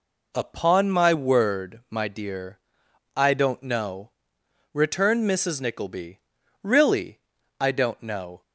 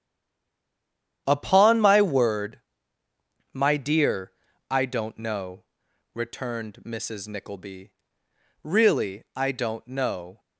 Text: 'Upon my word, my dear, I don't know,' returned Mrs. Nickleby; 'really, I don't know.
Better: first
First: none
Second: stays silent before the first word; noticeable; until 1.2 s; 1.2 s long // starts louder than the rest; strong; until 2.2 s; 9.5 dB

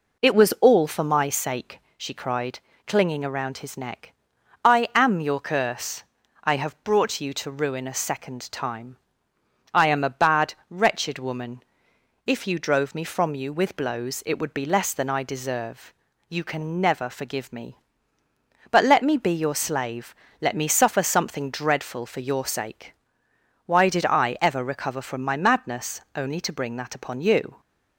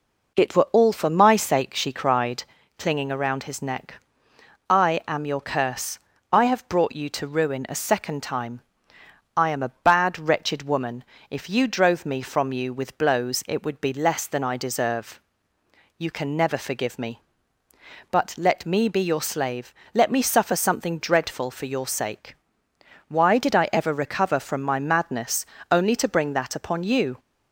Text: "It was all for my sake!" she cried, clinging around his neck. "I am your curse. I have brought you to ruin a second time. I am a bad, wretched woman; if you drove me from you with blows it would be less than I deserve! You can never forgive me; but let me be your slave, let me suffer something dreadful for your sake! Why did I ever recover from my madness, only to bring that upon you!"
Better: first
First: none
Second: says "were" for "was"; at 0.5 s

